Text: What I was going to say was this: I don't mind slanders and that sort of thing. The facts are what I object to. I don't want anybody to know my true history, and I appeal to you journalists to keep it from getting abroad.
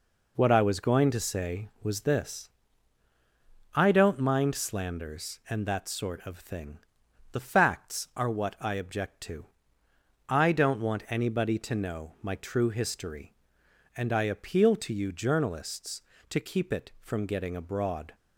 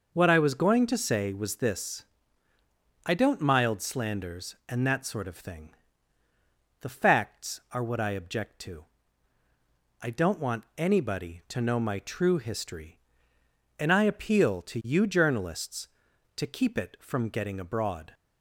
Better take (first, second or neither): first